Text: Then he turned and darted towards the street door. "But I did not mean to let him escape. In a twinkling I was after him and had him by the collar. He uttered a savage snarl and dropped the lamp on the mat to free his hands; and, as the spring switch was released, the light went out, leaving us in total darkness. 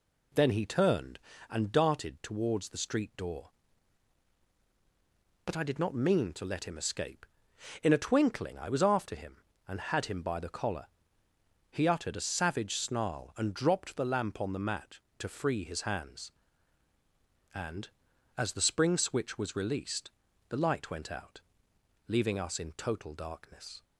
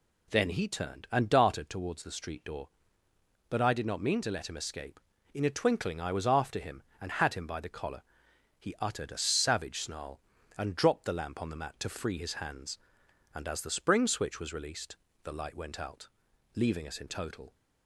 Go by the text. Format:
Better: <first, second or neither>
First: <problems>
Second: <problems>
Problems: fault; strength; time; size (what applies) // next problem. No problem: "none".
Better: first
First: none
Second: stops before "darkness"; at 17.5 s